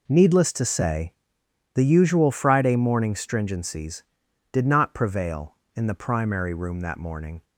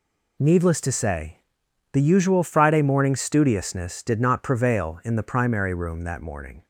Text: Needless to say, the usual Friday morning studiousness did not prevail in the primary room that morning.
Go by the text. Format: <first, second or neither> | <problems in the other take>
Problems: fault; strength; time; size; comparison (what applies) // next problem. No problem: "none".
second | says "stringencies" for "studiousness"; at 3.1 s